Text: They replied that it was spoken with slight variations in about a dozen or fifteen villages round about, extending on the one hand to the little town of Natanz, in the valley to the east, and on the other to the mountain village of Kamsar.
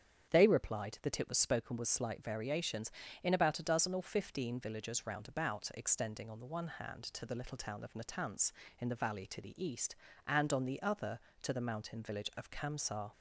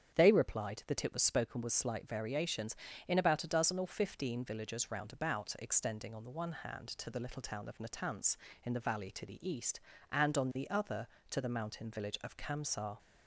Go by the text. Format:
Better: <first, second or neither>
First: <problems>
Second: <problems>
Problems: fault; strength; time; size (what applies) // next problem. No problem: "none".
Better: neither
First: starts louder than the rest; strong; until 1.3 s; 8 dB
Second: starts louder than the rest; strong; until 1.2 s; 8 dB